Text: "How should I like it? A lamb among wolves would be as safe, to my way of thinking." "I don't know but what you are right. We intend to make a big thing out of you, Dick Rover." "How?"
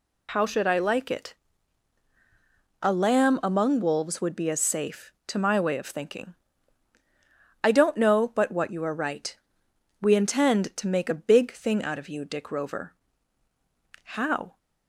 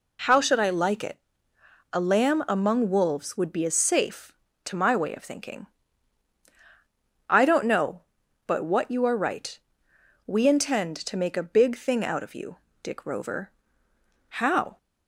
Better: neither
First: none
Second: none

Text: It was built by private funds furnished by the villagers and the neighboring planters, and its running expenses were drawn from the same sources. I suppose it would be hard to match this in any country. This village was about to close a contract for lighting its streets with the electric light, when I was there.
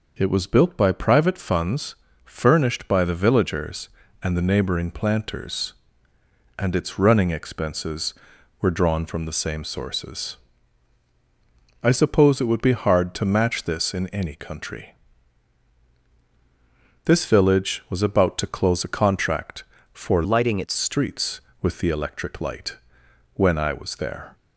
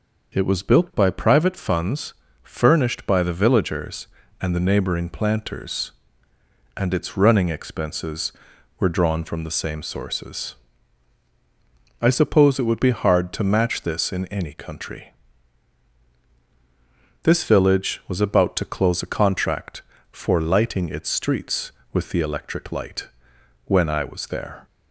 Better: second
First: pauses between "funds" and "furnished"; slight; at 1.9 s; 0.30 s long // changes voice from "lighting" to "its"; from 20.2 to 20.7 s; 0.5 s long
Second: pauses between "funds" and "furnished"; slight; at 2.1 s; 0.30 s long

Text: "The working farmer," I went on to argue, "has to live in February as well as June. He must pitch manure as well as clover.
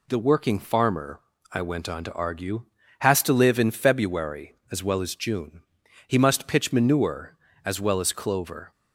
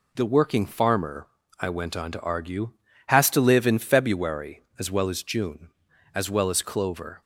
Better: first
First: none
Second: skips "He must pitch manure"; at 5.9 s

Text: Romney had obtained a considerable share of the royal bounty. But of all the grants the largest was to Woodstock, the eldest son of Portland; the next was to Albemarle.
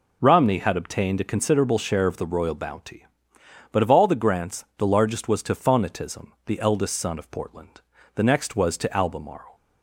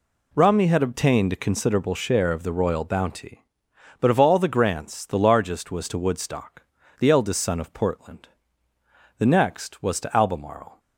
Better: second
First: says "Phonetism" for "Woodstock"; at 5.5 s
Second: none

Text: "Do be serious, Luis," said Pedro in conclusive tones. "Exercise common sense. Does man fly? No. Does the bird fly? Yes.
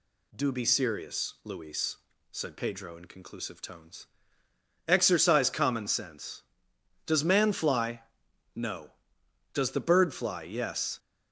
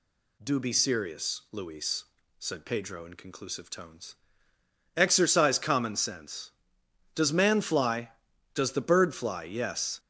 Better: first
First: none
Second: skips "No"; at 8.3 s

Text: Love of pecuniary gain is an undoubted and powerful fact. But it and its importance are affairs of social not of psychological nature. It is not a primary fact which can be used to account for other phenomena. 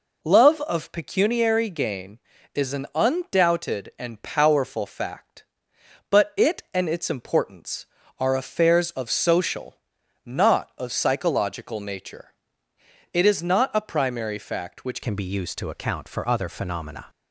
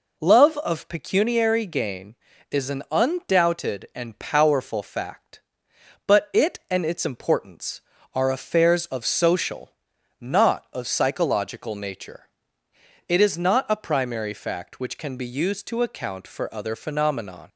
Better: second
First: pauses between "social" and "not"; noticeable; at 9.7 s; 0.54 s long // changes voice at "can"; from 15.0 s on; 2.0 s long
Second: pauses between "social" and "not"; noticeable; at 9.7 s; 0.54 s long

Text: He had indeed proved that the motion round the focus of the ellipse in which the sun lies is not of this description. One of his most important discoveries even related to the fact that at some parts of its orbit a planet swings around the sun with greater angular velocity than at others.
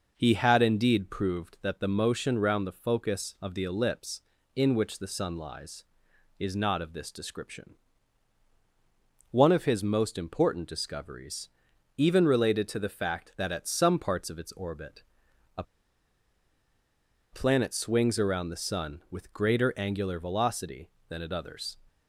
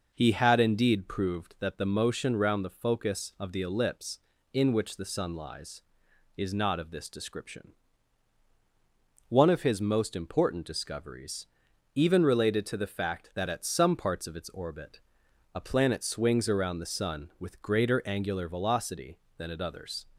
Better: second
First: pauses between "discoveries" and "even"; noticeable; at 11.4 s; 0.48 s long // pauses between "orbit" and "a"; noticeable; at 15.0 s; 0.54 s long // pauses between "a" and "planet"; strong; at 15.6 s; 1.6 s long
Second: pauses between "discoveries" and "even"; noticeable; at 11.4 s; 0.48 s long // pauses between "orbit" and "a"; noticeable; at 15.0 s; 0.54 s long

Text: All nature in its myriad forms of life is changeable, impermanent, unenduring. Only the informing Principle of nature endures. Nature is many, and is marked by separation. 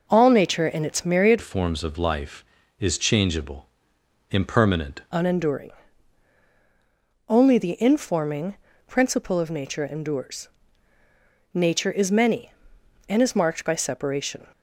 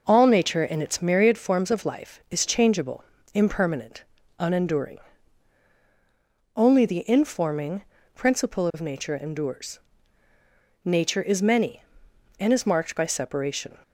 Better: second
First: changes voice from "forms" to "impermanent"; from 1.4 to 5.0 s; 3.6 s long // pauses between "informing" and "Principle"; slight; at 8.5 s; 0.34 s long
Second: pauses between "informing" and "Principle"; slight; at 7.8 s; 0.34 s long

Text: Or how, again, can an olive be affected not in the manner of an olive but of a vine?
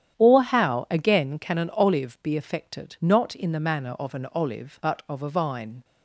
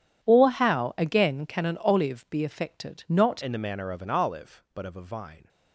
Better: first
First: starts louder than the rest; strong; until 1.2 s; 10 dB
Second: starts louder than the rest; strong; until 1.3 s; 10 dB // changes voice at "in"; from 3.4 s on; 2.0 s long

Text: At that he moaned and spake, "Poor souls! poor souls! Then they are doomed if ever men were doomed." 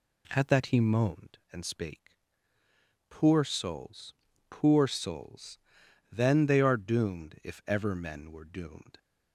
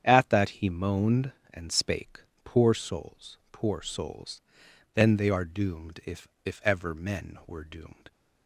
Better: first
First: none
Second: starts louder than the rest; strong; until 1.0 s; 8.5 dB // says "if" twice; at 6.4 s

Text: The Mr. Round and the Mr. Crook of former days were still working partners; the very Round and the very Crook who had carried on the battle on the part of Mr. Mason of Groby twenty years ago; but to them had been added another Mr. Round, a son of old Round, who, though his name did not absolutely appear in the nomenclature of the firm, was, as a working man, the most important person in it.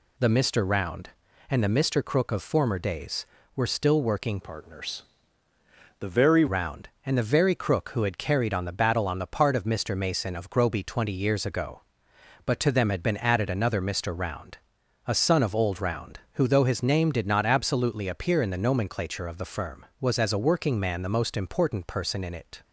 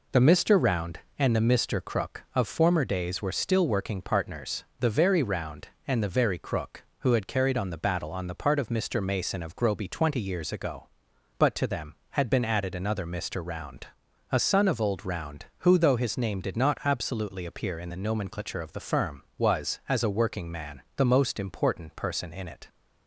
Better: second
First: changes voice from "partners" to "very"; from 4.4 to 6.4 s; 2.0 s long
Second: none

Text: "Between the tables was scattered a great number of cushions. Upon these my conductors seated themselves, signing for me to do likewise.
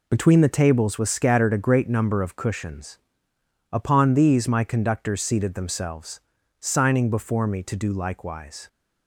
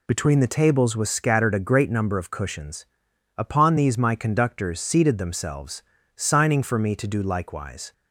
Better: second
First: says "before" for "for"; at 7.0 s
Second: none

